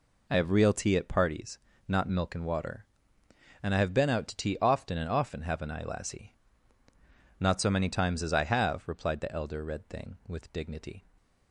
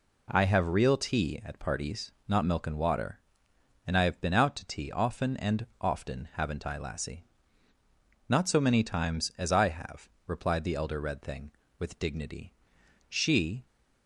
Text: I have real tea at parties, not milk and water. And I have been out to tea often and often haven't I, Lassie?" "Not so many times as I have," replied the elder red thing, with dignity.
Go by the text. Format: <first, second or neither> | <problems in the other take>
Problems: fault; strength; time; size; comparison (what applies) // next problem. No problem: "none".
first | pauses between "and" and "often"; slight; at 5.6 s; 0.16 s long // goes on to say "She"; from 13.0 s on; 0.56 s long